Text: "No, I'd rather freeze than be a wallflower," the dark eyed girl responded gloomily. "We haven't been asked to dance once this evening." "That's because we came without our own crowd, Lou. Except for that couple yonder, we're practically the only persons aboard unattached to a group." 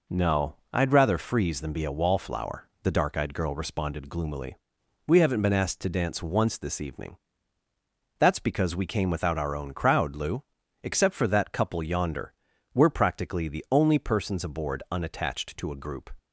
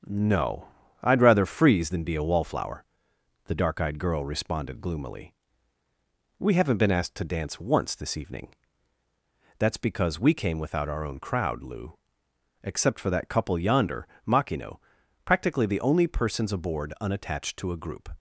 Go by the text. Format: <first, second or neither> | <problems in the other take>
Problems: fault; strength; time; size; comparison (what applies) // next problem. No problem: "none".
first | starts louder than the rest; strong; until 1.3 s; 7.5 dB // says "makino" for "we're"; at 14.2 s